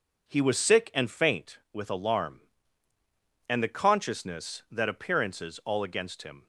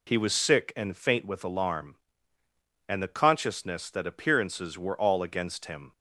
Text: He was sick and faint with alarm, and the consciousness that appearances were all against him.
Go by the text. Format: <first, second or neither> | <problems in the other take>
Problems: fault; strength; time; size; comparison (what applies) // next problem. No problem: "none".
second | skips "were"; at 5.6 s